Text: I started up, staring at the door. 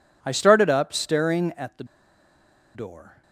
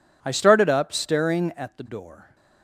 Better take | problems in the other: second | pauses between "the" and "door"; noticeable; at 1.8 s; 0.90 s long

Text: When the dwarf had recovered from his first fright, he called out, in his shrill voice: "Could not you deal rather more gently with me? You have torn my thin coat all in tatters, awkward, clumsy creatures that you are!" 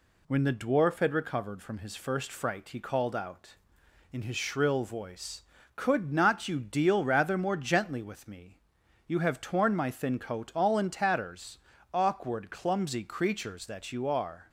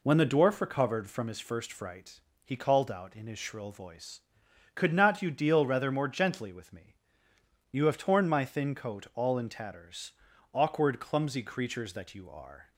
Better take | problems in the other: first | skips "had"; at 0.5 s

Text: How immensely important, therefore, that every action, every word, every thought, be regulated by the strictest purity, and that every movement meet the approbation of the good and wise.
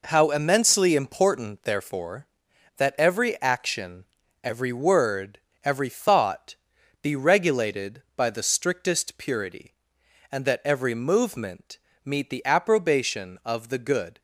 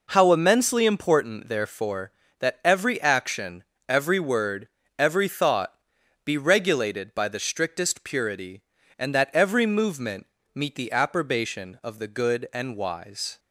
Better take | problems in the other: second | pauses between "movement" and "meet"; slight; at 11.7 s; 0.26 s long; slight in the second // stops before "and wise"; at 14.1 s

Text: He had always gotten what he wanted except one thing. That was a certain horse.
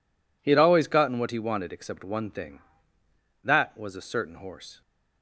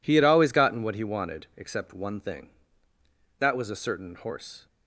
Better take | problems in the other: neither | none

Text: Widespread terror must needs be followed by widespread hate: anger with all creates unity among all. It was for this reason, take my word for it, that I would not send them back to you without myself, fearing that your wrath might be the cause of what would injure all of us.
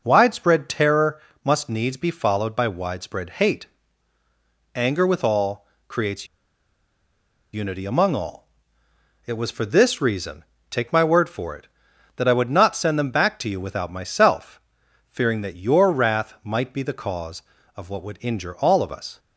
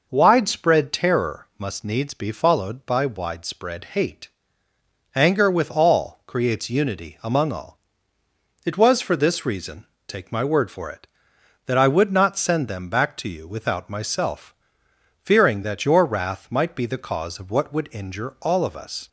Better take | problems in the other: second | pauses between "terror" and "must"; slight; at 1.2 s; 0.24 s long // pauses between "all" and "creates"; slight; at 5.6 s; 0.22 s long // pauses between "creates" and "unity"; strong; at 6.2 s; 1.2 s long

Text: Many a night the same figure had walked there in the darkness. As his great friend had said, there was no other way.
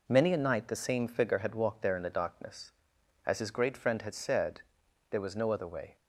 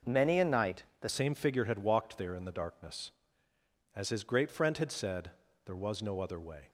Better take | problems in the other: first | pauses between "night" and "the"; slight; at 0.8 s; 0.16 s long // changes voice at "same"; from 1.0 s on; 5.6 s long

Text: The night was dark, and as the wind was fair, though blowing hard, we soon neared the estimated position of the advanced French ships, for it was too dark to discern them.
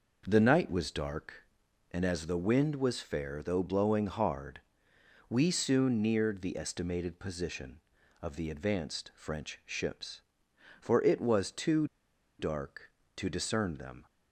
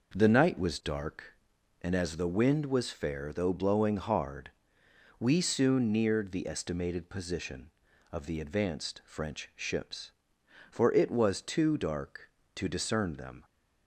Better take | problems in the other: second | pauses between "too" and "dark"; noticeable; at 11.8 s; 0.52 s long

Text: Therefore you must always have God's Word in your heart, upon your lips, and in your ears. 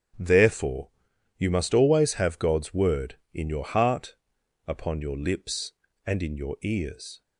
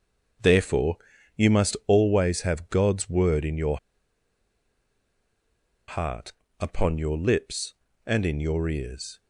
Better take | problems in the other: first | starts louder than the rest; until 1.9 s; 7 dB; strong in the first // pauses between "Therefore" and "you"; at 0.9 s; 0.38 s long; noticeable in the first // pauses between "your" and "heart"; strong; at 3.7 s; 2.1 s long

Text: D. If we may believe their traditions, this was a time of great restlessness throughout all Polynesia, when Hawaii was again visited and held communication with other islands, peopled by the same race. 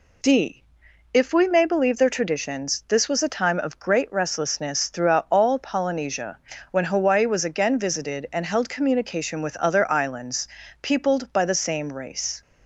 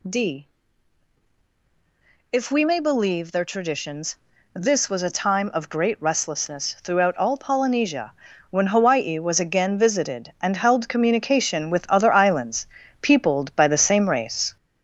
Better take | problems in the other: first | gets louder; noticeable; throughout; 5 dB

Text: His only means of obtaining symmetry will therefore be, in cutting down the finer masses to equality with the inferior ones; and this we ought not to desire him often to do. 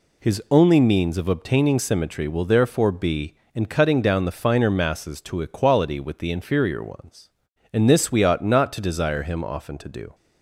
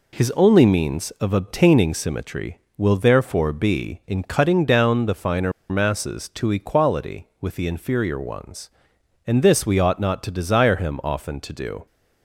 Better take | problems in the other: first | pauses between "finer" and "masses"; slight; at 5.5 s; 0.17 s long

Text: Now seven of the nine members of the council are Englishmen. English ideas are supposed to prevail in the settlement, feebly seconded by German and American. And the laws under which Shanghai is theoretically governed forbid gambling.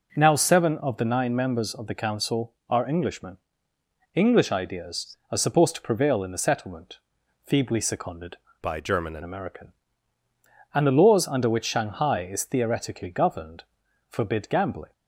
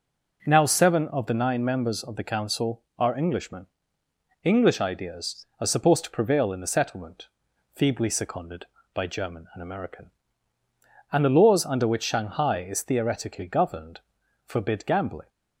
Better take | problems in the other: second | changes voice from "by" to "and"; from 8.6 to 9.2 s; 0.6 s long // pauses between "governed" and "forbid"; noticeable; at 13.6 s; 0.48 s long; noticeable in the second

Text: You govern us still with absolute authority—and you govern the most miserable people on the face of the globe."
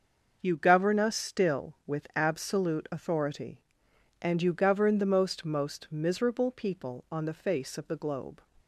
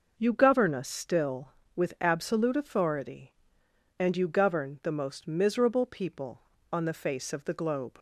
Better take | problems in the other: second | starts louder than the rest; noticeable; until 1.4 s; 6 dB // says "most" twice; at 5.4 s

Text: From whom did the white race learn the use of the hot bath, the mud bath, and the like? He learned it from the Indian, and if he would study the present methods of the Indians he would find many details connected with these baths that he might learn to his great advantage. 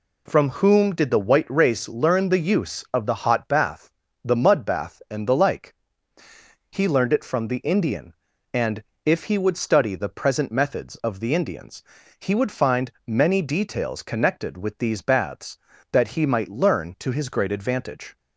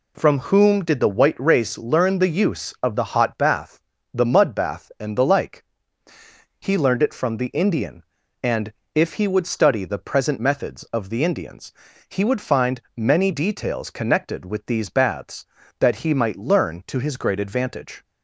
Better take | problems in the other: neither | pauses between "and" and "if"; slight; the same in both // pauses between "Indians" and "he"; slight; the same in both // pauses between "find" and "many"; slight; the same in both

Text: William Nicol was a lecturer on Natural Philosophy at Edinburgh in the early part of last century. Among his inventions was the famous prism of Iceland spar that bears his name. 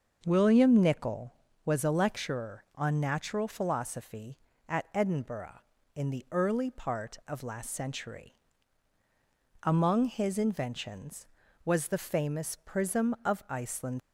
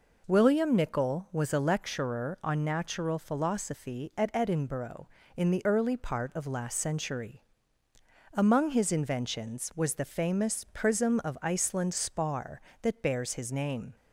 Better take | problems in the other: second | starts louder than the rest; noticeable; until 1.2 s; 6 dB // stops before "spar that bears his name"; at 13.9 s

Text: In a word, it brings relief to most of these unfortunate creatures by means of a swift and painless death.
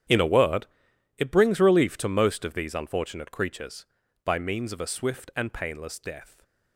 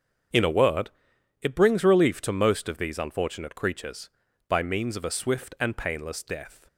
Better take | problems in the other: second | gets quieter; strong; throughout; 17 dB // starts louder than the rest; strong; until 1.5 s; 9.5 dB; also in the second

